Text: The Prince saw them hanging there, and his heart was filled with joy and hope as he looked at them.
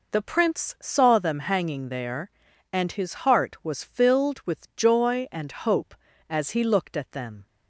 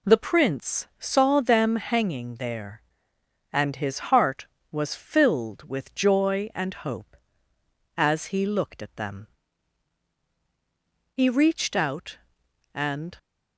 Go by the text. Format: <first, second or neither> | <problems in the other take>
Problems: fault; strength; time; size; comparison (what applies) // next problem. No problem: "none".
first | goes on to say "He reached out and"; strong; from 11.1 s on; 2.0 s long